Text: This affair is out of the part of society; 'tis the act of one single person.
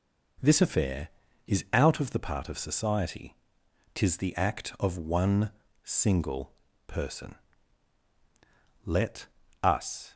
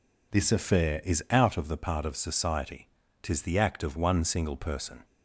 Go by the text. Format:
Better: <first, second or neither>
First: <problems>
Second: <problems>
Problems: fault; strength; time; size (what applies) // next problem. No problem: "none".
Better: second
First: pauses between "one" and "single"; noticeable; at 5.5 s; 0.50 s long // pauses between "single" and "person"; slight; at 6.5 s; 0.34 s long // goes on to say "Let us"; noticeable; from 8.8 s on; 1.2 s long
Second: none